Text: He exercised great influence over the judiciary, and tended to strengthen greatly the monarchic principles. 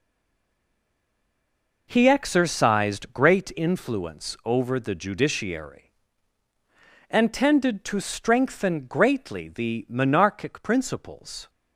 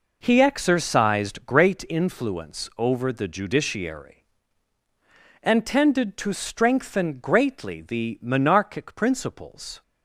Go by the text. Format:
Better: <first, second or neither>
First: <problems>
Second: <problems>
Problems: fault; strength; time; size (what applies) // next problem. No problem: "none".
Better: second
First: stays silent before the first word; noticeable; until 1.8 s; 1.8 s long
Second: none